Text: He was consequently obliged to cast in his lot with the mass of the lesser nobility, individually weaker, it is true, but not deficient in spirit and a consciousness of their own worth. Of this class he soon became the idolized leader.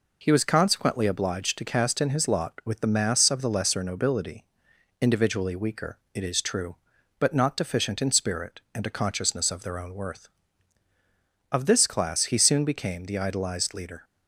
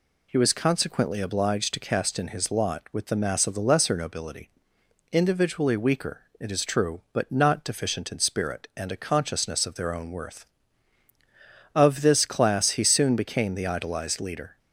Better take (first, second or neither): neither